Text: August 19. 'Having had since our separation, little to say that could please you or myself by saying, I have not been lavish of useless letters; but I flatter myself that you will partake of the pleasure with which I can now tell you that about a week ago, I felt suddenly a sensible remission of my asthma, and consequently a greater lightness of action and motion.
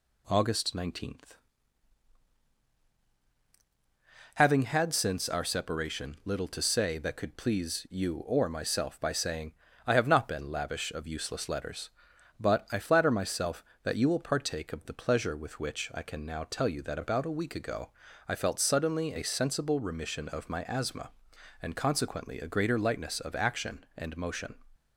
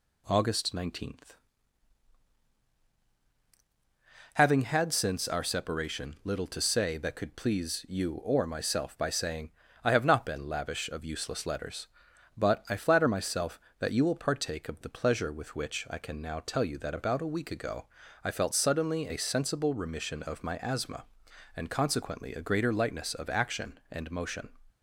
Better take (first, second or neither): neither